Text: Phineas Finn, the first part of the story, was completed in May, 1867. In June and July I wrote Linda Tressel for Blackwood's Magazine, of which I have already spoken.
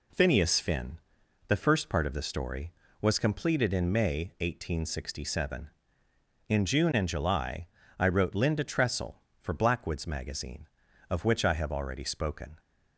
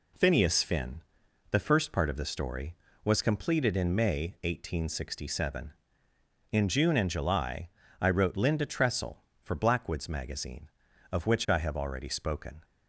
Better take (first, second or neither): neither